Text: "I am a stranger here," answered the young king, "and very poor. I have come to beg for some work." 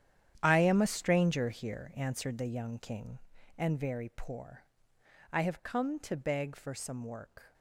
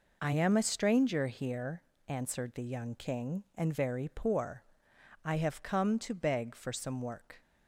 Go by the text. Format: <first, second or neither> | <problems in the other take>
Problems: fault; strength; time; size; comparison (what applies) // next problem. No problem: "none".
second | gets quieter; strong; throughout; 14 dB